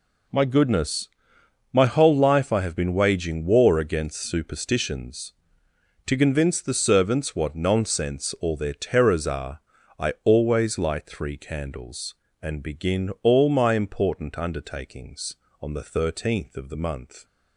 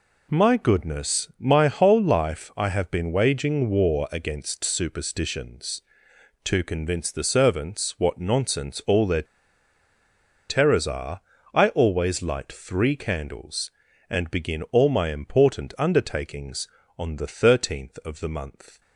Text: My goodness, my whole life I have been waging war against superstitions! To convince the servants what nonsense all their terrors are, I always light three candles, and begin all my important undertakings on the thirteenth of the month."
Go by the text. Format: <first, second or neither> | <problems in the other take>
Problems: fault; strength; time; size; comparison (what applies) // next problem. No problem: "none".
first | pauses between "their" and "terrors"; strong; at 9.2 s; 1.2 s long